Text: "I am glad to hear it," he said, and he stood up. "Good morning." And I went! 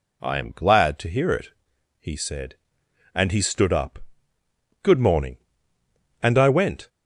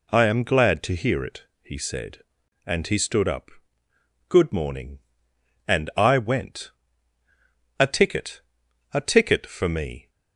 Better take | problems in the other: first | goes on to say "A ticket a ticket for me"; strong; from 7.7 s on; 2.3 s long

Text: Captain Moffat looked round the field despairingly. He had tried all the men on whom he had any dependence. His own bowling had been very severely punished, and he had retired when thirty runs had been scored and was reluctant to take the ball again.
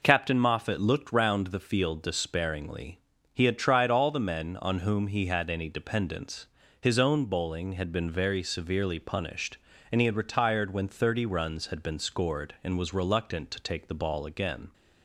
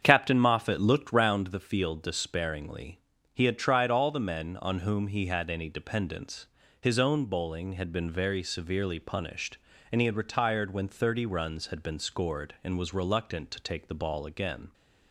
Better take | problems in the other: first | starts louder than the rest; strong; until 1.4 s; 7.5 dB

